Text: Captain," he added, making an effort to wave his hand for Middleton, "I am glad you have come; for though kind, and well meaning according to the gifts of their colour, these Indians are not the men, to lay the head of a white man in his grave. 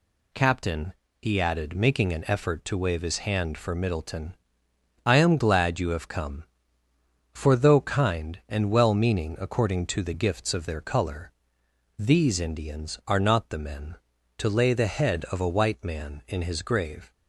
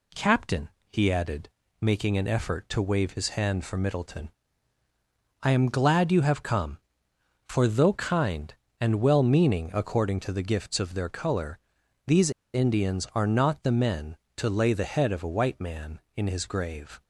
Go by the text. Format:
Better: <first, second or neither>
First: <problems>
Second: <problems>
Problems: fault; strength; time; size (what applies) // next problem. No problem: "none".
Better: first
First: none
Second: pauses between "these" and "Indians"; slight; at 12.3 s; 0.23 s long